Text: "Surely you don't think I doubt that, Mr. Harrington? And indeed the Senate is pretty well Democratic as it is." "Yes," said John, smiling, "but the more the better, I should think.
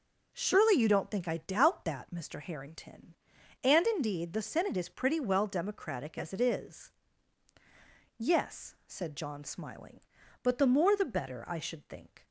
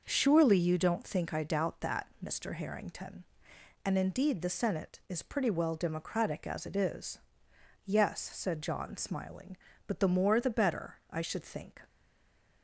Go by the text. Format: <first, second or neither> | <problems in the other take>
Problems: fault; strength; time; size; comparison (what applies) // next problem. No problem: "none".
first | stays silent after the last word; slight; from 11.8 s on; 0.8 s long